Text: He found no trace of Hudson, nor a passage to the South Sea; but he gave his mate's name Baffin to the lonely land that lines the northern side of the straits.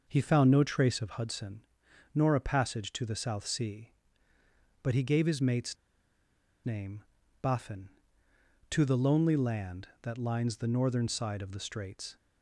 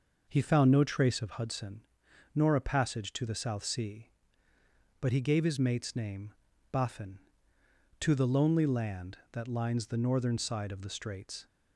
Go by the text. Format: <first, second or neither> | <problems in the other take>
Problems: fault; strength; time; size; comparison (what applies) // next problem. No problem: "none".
second | pauses between "mate's" and "name"; noticeable; at 5.7 s; 0.88 s long // pauses between "name" and "Baffin"; at 7.0 s; 0.38 s long; also in the second